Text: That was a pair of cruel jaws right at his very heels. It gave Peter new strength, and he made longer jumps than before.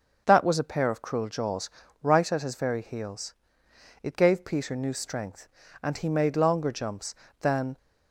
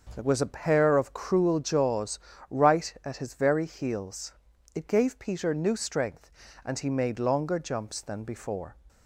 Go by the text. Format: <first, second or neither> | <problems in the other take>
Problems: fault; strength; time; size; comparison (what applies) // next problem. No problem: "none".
second | starts louder than the rest; until 1.2 s; 6 dB; also in the second // pauses between "jaws" and "right"; slight; at 1.7 s; 0.32 s long; slight in the second // stops before "before"; at 7.7 s